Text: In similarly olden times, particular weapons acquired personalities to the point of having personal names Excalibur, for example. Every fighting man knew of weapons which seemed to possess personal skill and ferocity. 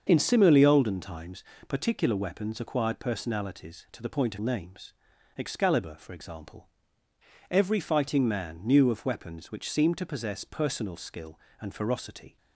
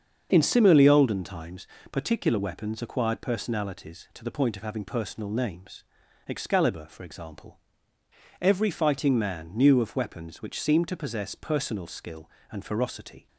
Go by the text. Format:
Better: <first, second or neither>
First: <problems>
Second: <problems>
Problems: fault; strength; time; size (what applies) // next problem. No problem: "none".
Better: second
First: starts louder than the rest; until 1.0 s; 7 dB // skips "having personal"; at 4.3 s // pauses between "names" and "Excalibur"; noticeable; at 4.9 s; 0.46 s long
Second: starts louder than the rest; until 1.3 s; 7 dB // pauses between "names" and "Excalibur"; noticeable; at 5.8 s; 0.46 s long